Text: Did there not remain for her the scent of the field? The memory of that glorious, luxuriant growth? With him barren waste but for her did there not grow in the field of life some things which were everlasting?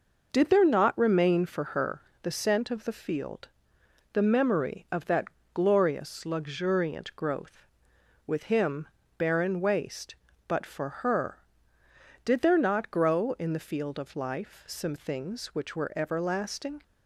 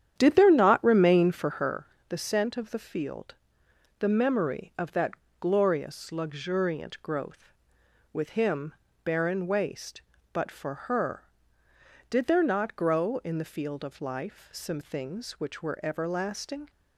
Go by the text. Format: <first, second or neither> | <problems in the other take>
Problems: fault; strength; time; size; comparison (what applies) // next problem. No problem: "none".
first | starts louder than the rest; strong; until 1.7 s; 9.5 dB // pauses between "her" and "the"; slight; at 1.8 s; 0.22 s long; slight in the first // pauses between "that" and "glorious"; slight; at 5.1 s; 0.26 s long; slight in the first // pauses between "him" and "barren"; slight; at 8.7 s; 0.30 s long; slight in the first